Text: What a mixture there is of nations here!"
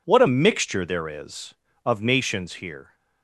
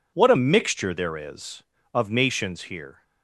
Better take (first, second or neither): neither